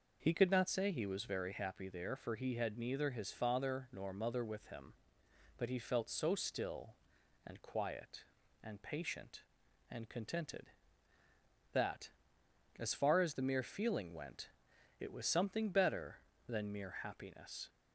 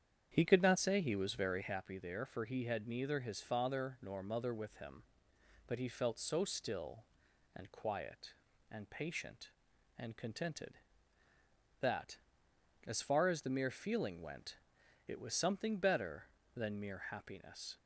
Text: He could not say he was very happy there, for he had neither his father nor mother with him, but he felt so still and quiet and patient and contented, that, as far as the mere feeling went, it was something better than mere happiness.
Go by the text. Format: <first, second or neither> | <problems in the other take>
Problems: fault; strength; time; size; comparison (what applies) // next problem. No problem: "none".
first | starts louder than the rest; strong; until 1.7 s; 8.5 dB